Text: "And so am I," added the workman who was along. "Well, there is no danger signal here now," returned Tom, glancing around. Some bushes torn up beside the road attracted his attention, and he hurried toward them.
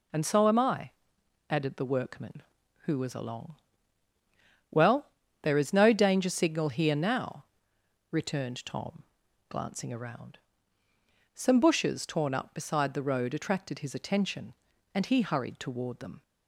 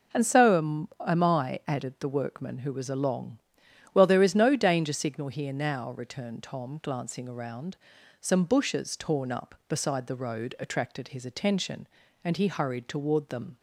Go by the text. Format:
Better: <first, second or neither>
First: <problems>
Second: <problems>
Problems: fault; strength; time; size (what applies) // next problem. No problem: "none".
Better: first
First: none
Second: says "am" twice; at 1.0 s